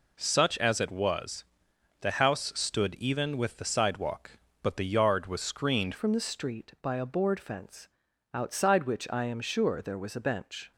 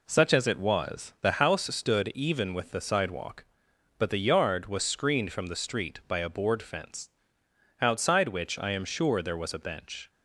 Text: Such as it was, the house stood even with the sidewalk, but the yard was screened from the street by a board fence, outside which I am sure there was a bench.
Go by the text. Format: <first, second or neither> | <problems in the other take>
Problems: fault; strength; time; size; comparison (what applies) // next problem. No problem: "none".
second | changes voice at "from"; from 5.9 s on; 4.8 s long